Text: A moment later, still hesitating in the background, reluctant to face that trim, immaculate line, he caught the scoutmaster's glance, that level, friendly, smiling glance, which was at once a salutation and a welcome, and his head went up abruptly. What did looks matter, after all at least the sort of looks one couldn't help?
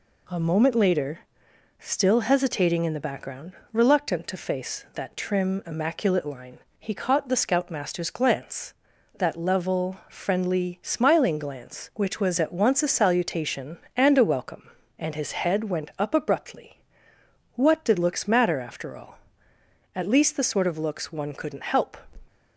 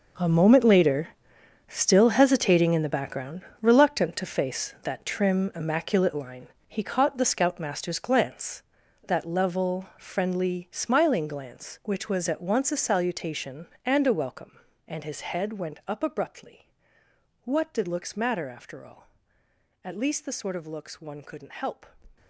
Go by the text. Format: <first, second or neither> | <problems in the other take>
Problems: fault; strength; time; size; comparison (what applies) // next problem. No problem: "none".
first | gets quieter; strong; throughout; 14 dB